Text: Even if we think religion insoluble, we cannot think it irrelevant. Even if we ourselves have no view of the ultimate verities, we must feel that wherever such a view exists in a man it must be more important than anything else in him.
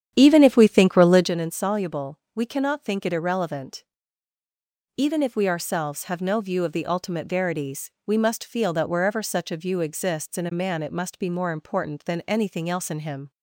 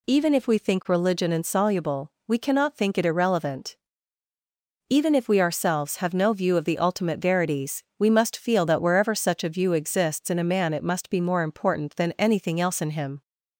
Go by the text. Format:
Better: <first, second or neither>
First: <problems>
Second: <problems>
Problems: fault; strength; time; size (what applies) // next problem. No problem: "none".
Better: second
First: starts louder than the rest; strong; until 1.3 s; 9.5 dB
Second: none